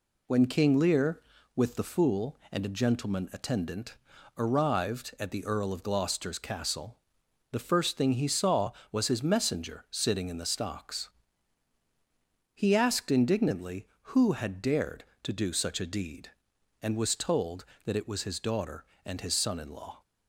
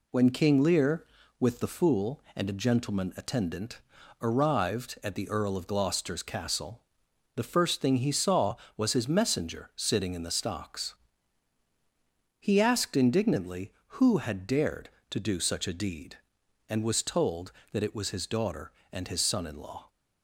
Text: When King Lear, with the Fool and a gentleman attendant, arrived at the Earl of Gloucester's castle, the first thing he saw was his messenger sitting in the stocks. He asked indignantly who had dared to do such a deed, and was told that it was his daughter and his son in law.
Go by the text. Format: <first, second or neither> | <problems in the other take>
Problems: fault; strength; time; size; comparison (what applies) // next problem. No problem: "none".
neither | none